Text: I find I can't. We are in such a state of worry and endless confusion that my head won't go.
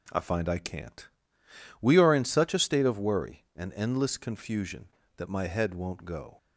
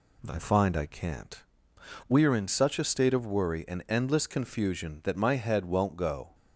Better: neither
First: none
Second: none

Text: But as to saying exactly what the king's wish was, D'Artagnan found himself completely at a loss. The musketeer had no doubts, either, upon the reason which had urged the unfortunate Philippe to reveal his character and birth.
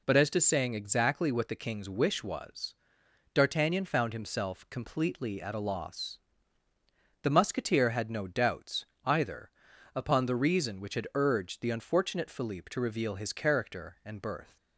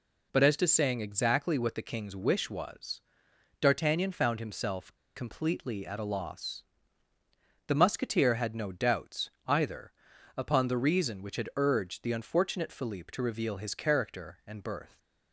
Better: first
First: none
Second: pauses between "himself" and "completely"; slight; at 4.9 s; 0.20 s long

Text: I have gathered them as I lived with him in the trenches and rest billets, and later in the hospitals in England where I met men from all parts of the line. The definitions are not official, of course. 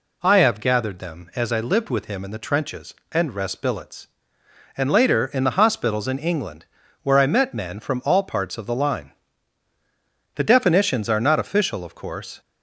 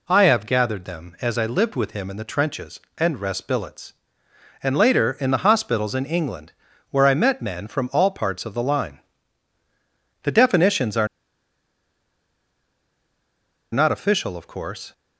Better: first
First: pauses between "England" and "where"; at 6.6 s; 0.37 s long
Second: pauses between "England" and "where"; at 6.5 s; 0.38 s long // pauses between "are" and "not"; strong; at 11.0 s; 2.6 s long

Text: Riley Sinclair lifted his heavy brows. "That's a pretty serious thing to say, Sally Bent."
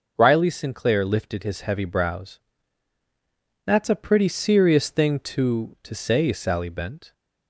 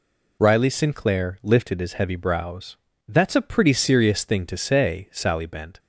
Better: second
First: says "to" twice; at 5.8 s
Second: none

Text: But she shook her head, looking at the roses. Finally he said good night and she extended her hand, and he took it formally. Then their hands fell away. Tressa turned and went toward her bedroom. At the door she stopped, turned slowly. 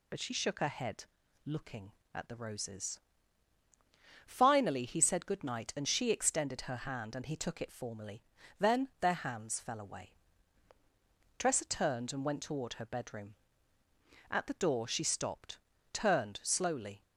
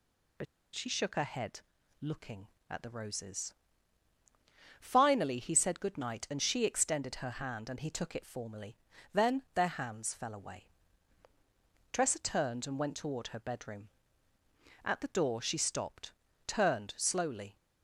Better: first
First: none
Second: pauses between "But" and "she"; slight; at 0.4 s; 0.30 s long

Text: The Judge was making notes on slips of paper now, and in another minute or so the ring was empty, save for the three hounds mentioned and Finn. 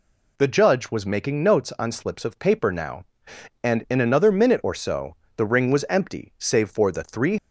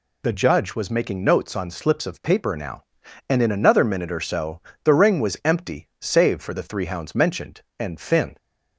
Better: second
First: pauses between "so" and "the"; slight; at 5.1 s; 0.18 s long // stops before "hounds mentioned and Finn"; at 7.3 s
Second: pauses between "so" and "the"; slight; at 4.5 s; 0.22 s long

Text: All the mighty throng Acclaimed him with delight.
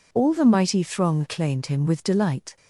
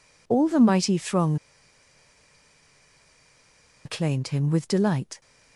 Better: first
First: none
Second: pauses between "throng" and "Acclaimed"; strong; at 1.3 s; 2.4 s long

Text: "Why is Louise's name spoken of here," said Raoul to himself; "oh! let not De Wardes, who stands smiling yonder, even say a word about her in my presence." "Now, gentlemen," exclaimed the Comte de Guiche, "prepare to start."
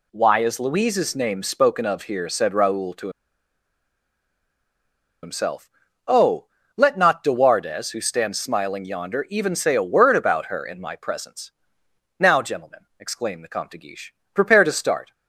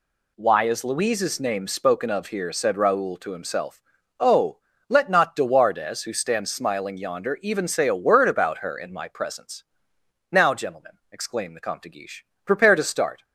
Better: second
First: pauses between "to" and "himself"; strong; at 3.0 s; 2.1 s long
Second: none

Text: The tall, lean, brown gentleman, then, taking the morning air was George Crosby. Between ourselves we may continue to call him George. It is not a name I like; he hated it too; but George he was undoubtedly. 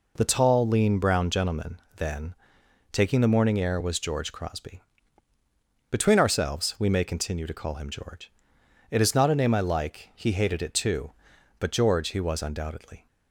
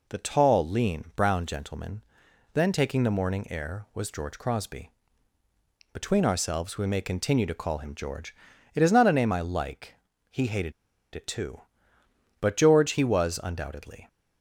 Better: first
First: none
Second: pauses between "hated" and "it"; at 10.7 s; 0.42 s long

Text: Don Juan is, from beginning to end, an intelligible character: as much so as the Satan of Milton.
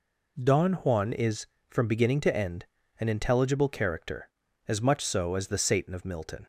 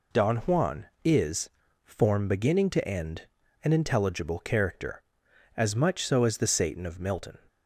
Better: first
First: none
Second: says "form" for "from"; at 1.8 s

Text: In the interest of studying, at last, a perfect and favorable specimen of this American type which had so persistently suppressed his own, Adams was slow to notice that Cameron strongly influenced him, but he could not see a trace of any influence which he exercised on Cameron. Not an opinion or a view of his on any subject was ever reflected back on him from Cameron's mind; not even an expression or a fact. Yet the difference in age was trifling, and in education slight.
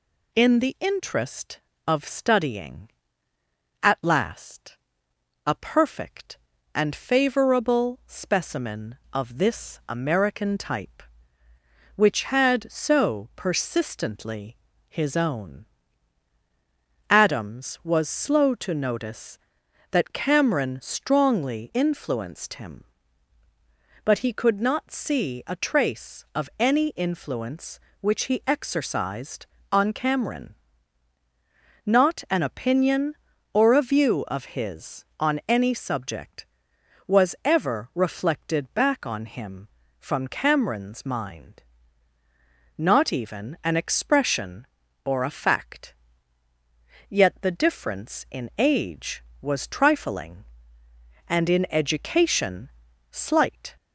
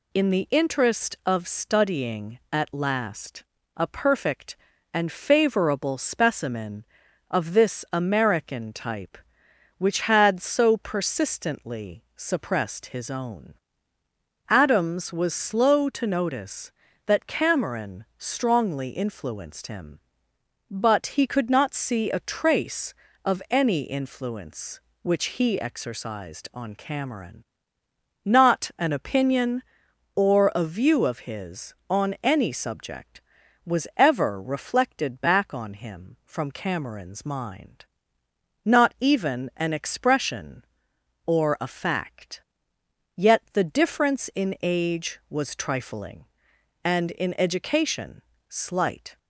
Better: second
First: skips "suppressed"; at 14.7 s // pauses between "education" and "slight"; at 52.6 s; 0.42 s long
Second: pauses between "education" and "slight"; slight; at 48.2 s; 0.28 s long

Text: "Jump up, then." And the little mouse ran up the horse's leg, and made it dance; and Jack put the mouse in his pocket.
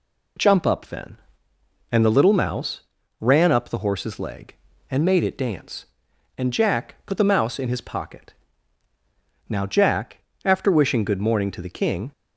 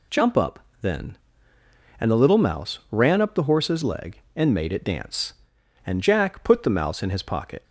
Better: second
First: pauses between "mouse" and "ran"; at 2.8 s; 0.38 s long // goes on to say "Now Jack after wishing good morning to the King"; strong; from 9.4 s on; 2.6 s long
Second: none

